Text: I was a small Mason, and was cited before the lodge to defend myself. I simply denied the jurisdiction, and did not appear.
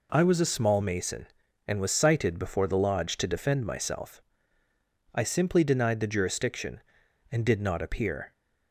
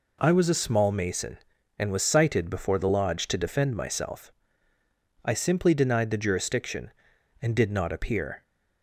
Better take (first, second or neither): neither